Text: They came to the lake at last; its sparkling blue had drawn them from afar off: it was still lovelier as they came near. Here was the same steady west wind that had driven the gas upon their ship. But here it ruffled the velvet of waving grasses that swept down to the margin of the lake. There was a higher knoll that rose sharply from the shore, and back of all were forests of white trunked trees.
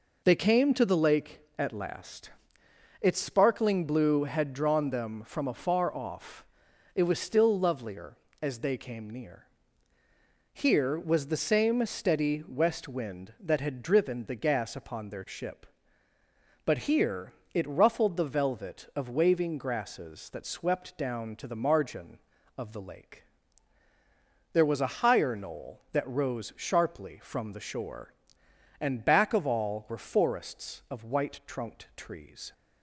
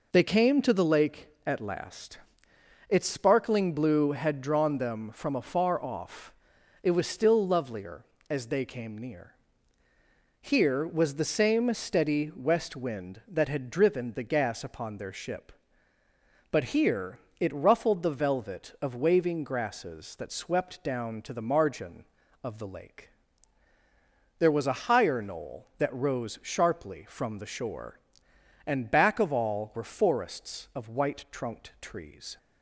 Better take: neither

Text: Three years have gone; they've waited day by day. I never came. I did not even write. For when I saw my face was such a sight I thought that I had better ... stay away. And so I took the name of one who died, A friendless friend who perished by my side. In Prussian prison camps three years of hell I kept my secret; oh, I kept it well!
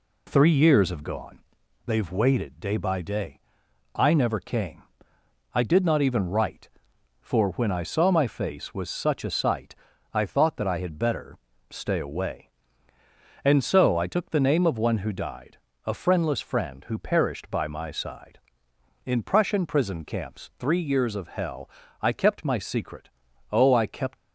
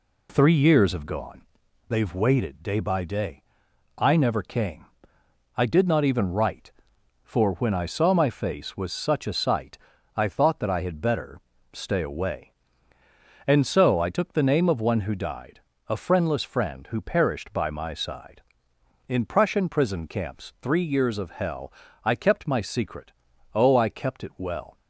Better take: second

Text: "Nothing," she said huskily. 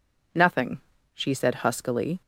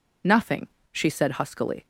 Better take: neither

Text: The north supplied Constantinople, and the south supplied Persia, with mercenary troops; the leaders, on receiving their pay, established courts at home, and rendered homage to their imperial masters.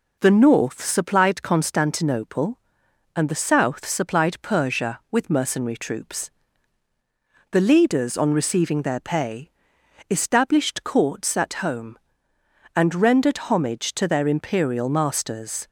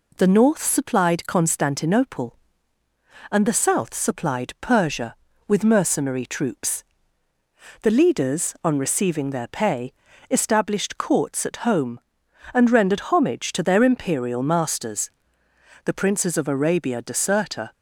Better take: first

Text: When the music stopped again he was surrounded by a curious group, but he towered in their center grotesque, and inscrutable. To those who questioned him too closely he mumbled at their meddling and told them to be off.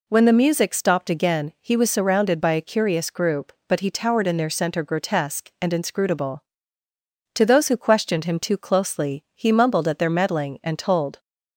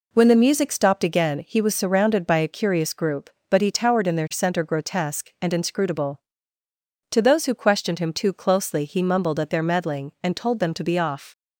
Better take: second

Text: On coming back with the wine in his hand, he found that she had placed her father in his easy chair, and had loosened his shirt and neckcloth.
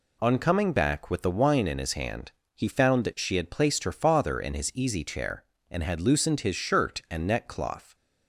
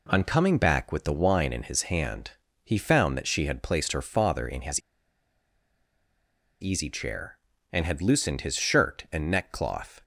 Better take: first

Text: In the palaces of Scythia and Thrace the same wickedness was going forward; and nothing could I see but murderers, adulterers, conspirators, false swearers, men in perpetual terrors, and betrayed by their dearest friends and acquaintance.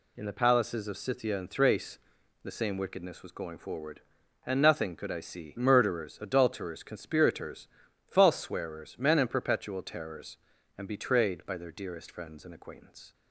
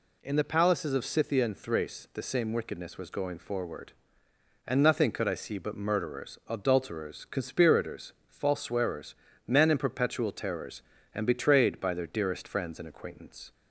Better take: second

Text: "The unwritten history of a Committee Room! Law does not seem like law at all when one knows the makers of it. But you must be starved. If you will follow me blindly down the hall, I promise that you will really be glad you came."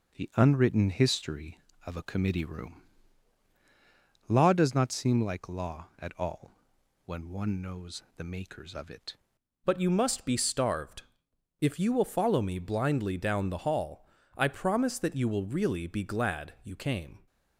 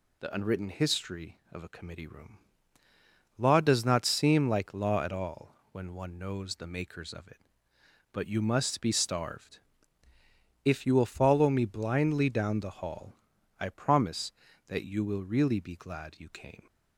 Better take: second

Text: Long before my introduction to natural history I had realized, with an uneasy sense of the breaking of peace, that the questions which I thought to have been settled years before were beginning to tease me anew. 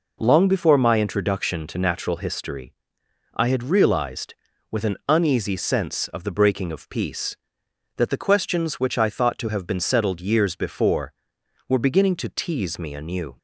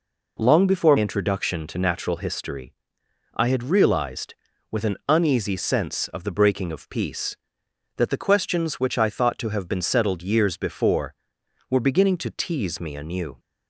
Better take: first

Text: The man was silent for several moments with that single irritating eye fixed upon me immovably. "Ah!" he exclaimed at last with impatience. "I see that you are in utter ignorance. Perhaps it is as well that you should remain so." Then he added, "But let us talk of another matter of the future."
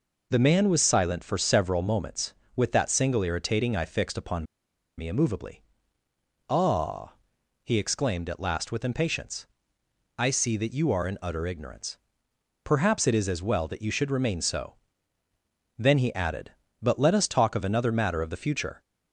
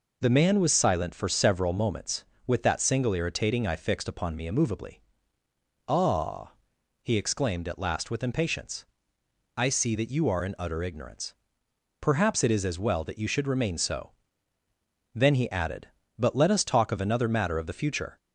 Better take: second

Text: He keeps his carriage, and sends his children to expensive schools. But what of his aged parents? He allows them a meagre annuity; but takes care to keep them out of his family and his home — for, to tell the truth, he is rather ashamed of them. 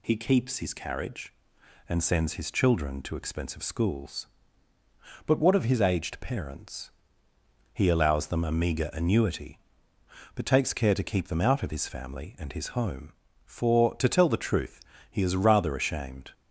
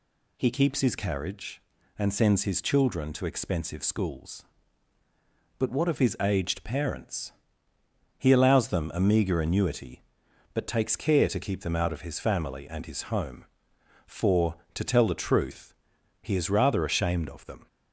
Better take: second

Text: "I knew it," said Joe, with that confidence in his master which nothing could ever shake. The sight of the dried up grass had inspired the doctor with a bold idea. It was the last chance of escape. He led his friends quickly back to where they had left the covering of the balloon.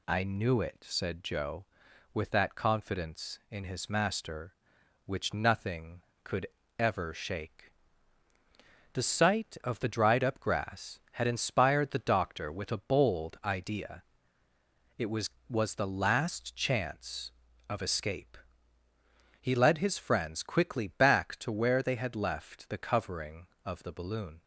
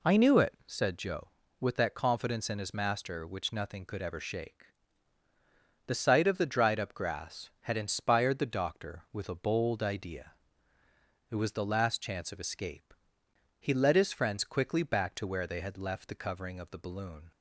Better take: second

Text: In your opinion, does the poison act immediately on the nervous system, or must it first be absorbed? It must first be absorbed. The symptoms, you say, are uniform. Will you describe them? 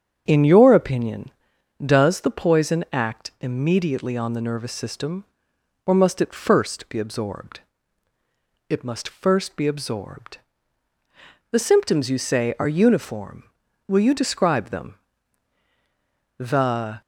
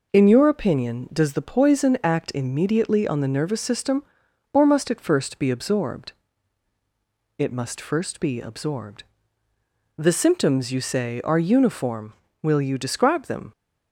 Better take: second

